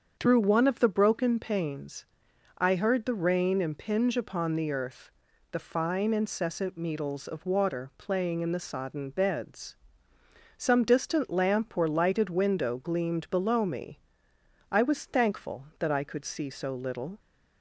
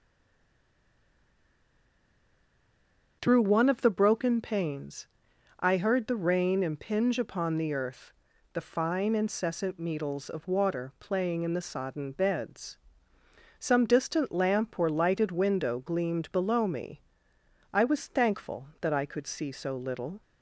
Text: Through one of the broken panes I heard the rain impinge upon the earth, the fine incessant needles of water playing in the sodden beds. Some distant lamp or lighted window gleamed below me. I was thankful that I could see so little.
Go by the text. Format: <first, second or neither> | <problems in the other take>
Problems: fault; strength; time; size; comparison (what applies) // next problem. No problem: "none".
first | stays silent before the first word; strong; until 3.2 s; 3.2 s long // starts louder than the rest; strong; until 4.2 s; 7.5 dB; strong in the first // pauses between "panes" and "I"; noticeable; at 5.0 s; 0.52 s long; noticeable in the first